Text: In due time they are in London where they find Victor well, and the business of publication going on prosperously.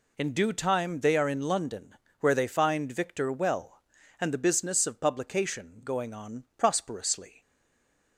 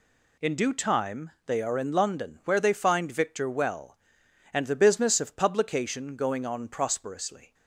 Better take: second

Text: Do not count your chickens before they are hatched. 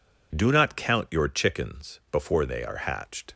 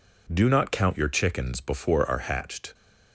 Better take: first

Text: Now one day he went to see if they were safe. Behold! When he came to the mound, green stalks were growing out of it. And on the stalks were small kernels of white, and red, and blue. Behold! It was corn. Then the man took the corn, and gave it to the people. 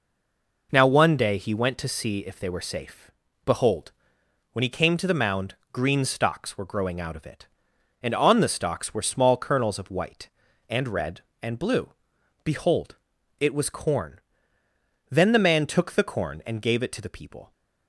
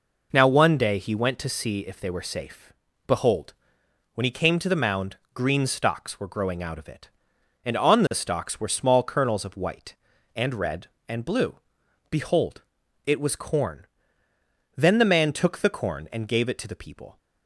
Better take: second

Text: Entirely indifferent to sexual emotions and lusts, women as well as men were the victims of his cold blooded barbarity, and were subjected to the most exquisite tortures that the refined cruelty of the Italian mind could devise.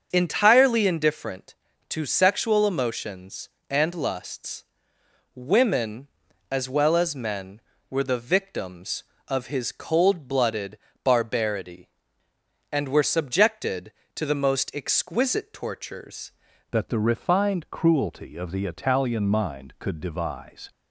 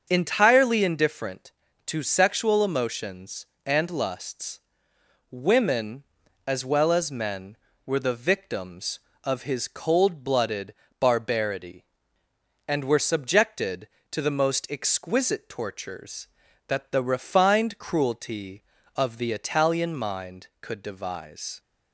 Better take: second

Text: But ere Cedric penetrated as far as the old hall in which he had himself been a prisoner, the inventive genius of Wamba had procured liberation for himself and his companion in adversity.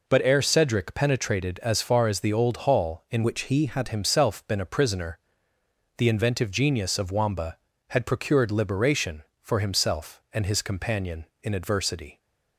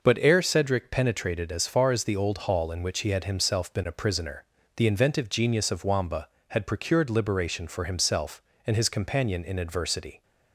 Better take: second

